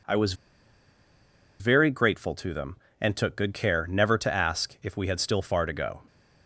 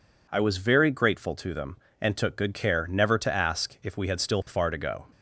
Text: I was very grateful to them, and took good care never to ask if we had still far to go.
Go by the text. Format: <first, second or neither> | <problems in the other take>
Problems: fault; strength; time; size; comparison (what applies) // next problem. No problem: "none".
second | pauses between "was" and "very"; strong; at 0.3 s; 1.2 s long